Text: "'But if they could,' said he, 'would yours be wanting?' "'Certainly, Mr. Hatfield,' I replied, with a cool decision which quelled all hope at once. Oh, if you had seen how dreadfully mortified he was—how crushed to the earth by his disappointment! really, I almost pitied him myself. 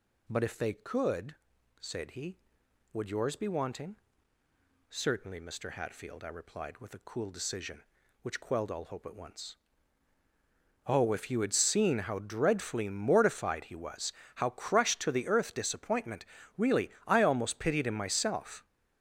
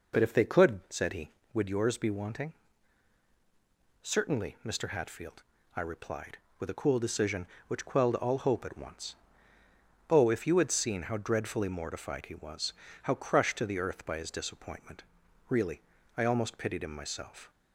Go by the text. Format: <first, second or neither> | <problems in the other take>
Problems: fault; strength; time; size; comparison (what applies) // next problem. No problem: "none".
second | skips "by his"; at 15.5 s